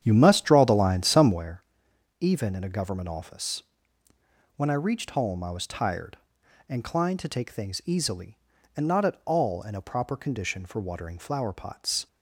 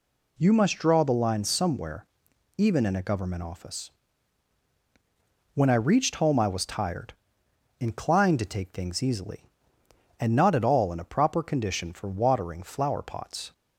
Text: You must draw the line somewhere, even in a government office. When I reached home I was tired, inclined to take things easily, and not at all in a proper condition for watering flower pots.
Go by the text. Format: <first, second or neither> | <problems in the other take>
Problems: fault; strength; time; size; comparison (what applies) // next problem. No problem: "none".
second | starts louder than the rest; strong; until 1.4 s; 9 dB